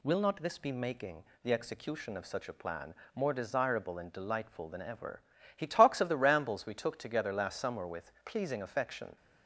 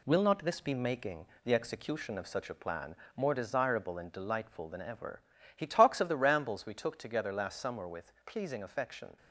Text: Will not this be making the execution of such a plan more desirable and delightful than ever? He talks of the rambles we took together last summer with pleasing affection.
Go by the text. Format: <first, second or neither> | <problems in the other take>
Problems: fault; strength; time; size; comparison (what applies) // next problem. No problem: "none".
first | gets quieter; noticeable; throughout; 4.5 dB // pauses between "making" and "the"; slight; at 1.2 s; 0.18 s long; slight in the first // pauses between "plan" and "more"; slight; at 2.9 s; 0.20 s long; slight in the first